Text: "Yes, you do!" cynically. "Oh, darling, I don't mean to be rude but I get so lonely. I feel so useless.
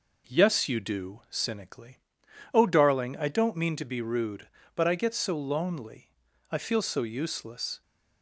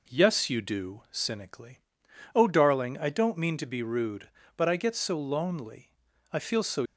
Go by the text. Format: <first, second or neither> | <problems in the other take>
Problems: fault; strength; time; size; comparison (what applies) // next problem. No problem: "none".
first | stops before "useless"; at 6.8 s